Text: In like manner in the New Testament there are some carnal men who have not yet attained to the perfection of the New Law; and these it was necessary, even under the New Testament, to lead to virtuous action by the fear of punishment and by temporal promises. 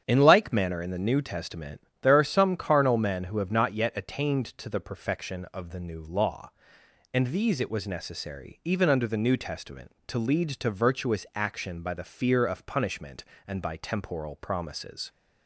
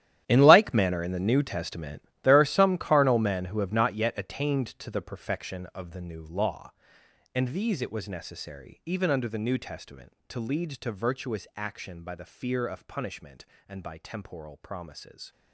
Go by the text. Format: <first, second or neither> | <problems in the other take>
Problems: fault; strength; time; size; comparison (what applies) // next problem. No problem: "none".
first | gets quieter; strong; throughout; 16 dB // starts louder than the rest; strong; until 1.2 s; 11.5 dB; strong in the first // pauses between "Testament" and "there"; slight; at 2.0 s; 0.22 s long; slight in the first